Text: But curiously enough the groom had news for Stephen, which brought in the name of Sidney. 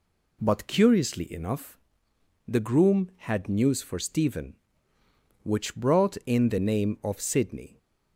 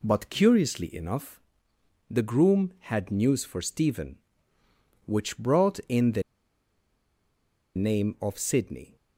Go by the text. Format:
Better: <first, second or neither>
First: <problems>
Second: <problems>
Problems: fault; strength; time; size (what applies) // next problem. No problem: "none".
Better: first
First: pauses between "enough" and "the"; noticeable; at 1.7 s; 0.70 s long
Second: pauses between "enough" and "the"; noticeable; at 1.3 s; 0.70 s long // pauses between "the" and "name"; strong; at 6.2 s; 1.5 s long